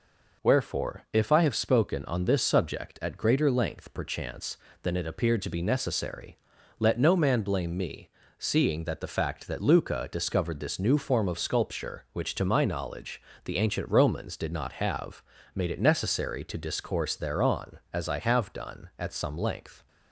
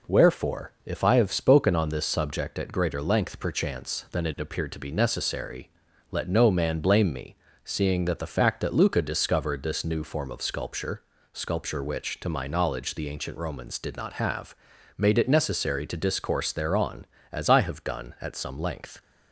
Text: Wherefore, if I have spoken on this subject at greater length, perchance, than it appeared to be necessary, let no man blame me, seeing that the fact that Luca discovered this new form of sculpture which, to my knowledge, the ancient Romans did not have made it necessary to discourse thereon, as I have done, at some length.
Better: first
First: pauses between "have" and "made"; slight; at 15.2 s; 0.31 s long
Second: says "sculpture" twice; at 11.3 s // pauses between "have" and "made"; at 14.5 s; 0.42 s long

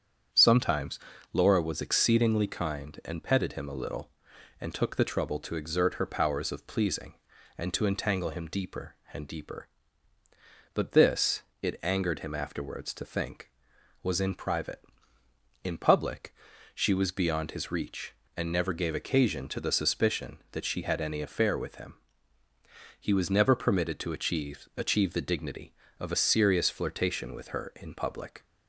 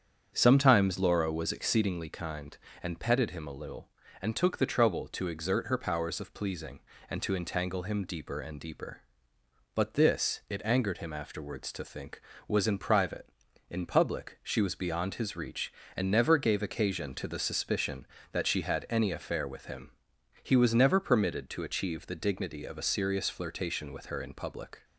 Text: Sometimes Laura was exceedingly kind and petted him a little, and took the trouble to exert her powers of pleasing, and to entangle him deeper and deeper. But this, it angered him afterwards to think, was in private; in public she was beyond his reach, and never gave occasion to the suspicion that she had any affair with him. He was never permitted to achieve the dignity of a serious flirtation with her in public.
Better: second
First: starts louder than the rest; strong; until 1.7 s; 8 dB // pauses between "Sometimes" and "Laura"; slight; at 0.9 s; 0.36 s long // pauses between "public" and "she"; at 16.3 s; 0.40 s long // says "achieve" twice; at 24.7 s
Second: starts louder than the rest; strong; until 1.3 s; 8 dB

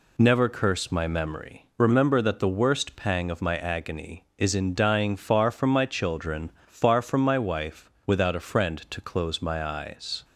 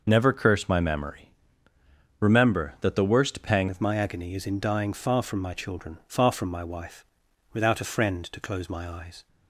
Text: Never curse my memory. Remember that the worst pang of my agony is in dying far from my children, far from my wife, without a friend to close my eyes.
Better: first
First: none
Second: changes voice at "of"; from 3.6 s on; 5.6 s long

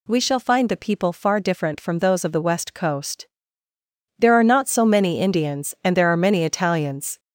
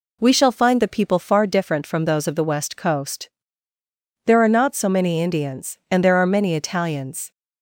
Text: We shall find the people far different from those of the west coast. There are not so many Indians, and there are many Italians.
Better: second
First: gets louder; noticeable; throughout; 4.5 dB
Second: none

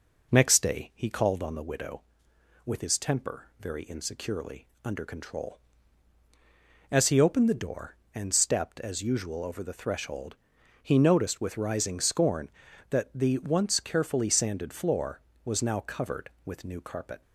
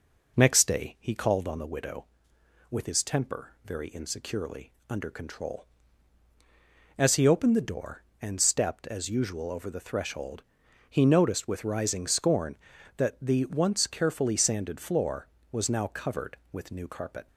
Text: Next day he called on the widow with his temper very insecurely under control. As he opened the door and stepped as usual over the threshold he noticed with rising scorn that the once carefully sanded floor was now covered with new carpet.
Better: neither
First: pauses between "insecurely" and "under"; slight; at 4.6 s; 0.16 s long // pauses between "threshold" and "he"; noticeable; at 10.3 s; 0.46 s long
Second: pauses between "insecurely" and "under"; slight; at 4.7 s; 0.16 s long // pauses between "threshold" and "he"; noticeable; at 10.4 s; 0.46 s long

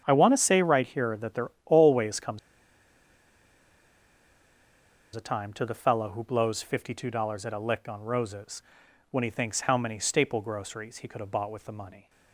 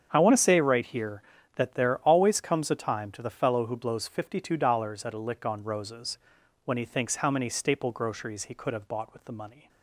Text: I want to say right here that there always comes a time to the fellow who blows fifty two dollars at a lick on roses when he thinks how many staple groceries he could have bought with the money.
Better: second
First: starts louder than the rest; strong; until 1.0 s; 8.5 dB // pauses between "there" and "always"; slight; at 1.4 s; 0.16 s long // pauses between "comes" and "a"; strong; at 2.3 s; 2.7 s long // pauses between "roses" and "when"; noticeable; at 8.6 s; 0.48 s long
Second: starts louder than the rest; strong; until 1.1 s; 7.5 dB // pauses between "roses" and "when"; noticeable; at 6.1 s; 0.48 s long

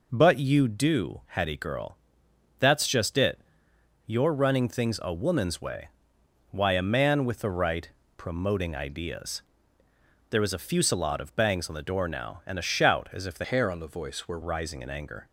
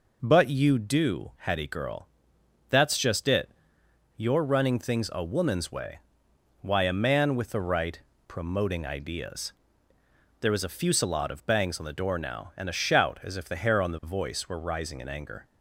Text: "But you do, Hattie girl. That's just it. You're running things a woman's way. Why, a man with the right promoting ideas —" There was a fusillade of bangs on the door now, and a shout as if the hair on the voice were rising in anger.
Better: second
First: pauses between "right" and "promoting"; slight; at 7.8 s; 0.28 s long // changes voice from "hair" to "were"; from 13.4 to 14.3 s; 0.9 s long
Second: pauses between "right" and "promoting"; slight; at 7.9 s; 0.28 s long

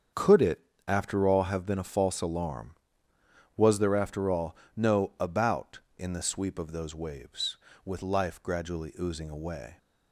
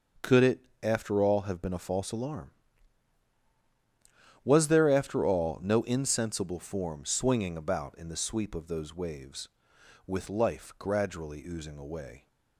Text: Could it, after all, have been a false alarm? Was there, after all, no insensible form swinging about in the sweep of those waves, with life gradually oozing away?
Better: second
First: starts louder than the rest; strong; until 1.4 s; 7 dB // skips "insensible form swinging"; at 5.1 s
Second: starts louder than the rest; until 1.3 s; 6.5 dB

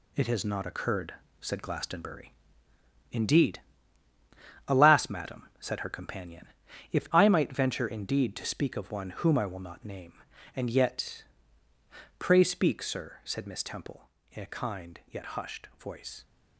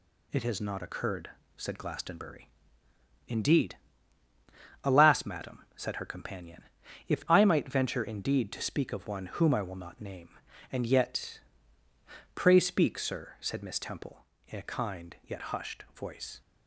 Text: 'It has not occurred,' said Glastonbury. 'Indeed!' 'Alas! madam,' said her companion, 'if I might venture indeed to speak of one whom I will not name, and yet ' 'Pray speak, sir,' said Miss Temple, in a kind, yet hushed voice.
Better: second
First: gets quieter; strong; throughout; 8 dB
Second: none

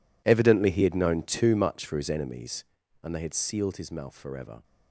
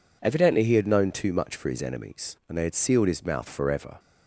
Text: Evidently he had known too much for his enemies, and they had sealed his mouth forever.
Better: second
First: gets quieter; strong; throughout; 17.5 dB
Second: none

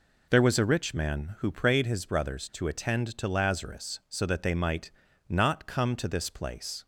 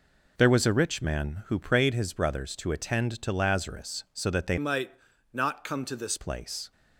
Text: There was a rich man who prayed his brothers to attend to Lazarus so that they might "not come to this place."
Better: first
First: pauses between "might" and "not"; at 4.8 s; 0.38 s long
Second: changes voice from "might" to "this"; from 4.5 to 6.1 s; 1.6 s long // pauses between "might" and "not"; at 4.9 s; 0.42 s long

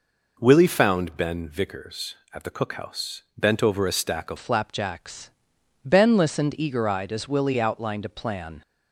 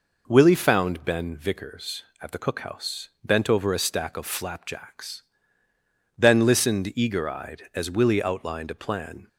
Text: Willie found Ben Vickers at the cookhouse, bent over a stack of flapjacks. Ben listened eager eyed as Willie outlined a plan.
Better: second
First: changes voice at "flapjacks"; from 4.3 s on; 4.3 s long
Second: none

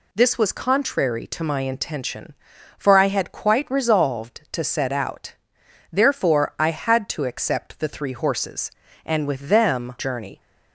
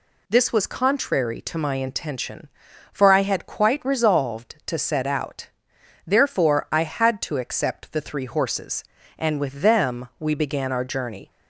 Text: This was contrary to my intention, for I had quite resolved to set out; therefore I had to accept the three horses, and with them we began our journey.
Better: second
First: skips "we began our"; at 9.9 s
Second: none

